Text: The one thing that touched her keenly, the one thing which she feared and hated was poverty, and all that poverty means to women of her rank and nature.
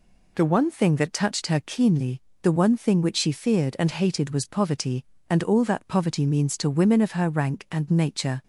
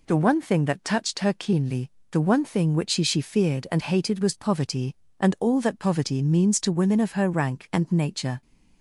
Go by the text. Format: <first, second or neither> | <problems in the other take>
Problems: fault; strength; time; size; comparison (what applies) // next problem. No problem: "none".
first | says "she" twice; at 3.0 s